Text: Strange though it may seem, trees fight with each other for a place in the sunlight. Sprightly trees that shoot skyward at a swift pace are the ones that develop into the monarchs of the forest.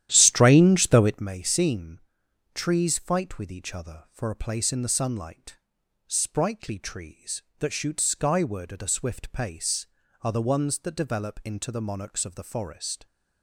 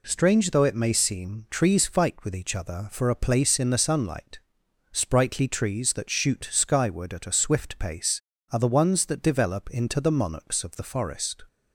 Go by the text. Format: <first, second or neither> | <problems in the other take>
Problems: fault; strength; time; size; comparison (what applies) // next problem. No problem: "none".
second | starts louder than the rest; strong; until 1.3 s; 11.5 dB